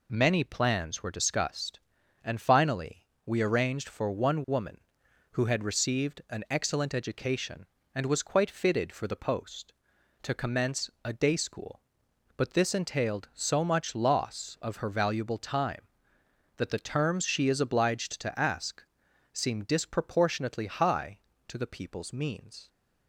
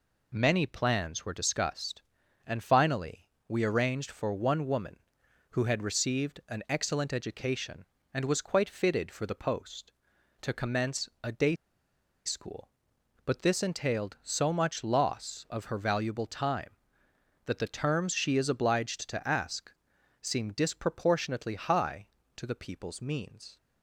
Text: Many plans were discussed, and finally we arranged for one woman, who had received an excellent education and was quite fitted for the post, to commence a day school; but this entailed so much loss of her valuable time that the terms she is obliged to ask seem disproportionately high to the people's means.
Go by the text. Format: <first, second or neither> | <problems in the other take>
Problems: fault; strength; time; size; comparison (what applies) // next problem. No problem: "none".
first | pauses between "finally" and "we"; slight; at 3.2 s; 0.18 s long; slight in the first // pauses between "commence" and "a"; slight; at 11.0 s; 0.16 s long; slight in the first // pauses between "day" and "school"; noticeable; at 11.5 s; 0.72 s long // pauses between "ask" and "seem"; noticeable; at 19.7 s; 0.48 s long; noticeable in the first